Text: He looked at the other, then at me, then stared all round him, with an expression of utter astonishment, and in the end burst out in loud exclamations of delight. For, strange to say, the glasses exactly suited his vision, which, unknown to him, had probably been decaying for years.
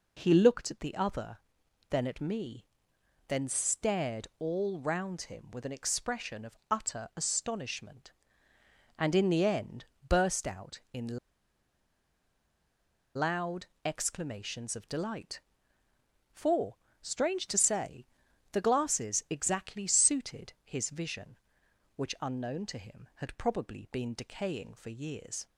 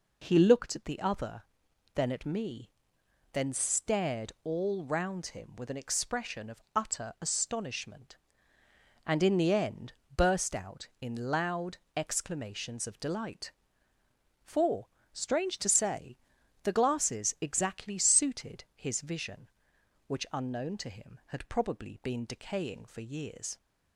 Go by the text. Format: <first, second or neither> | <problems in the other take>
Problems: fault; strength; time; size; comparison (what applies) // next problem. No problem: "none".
second | pauses between "end" and "burst"; slight; at 9.8 s; 0.22 s long; slight in the second // pauses between "in" and "loud"; strong; at 11.1 s; 1.9 s long // pauses between "loud" and "exclamations"; slight; at 13.6 s; 0.18 s long; slight in the second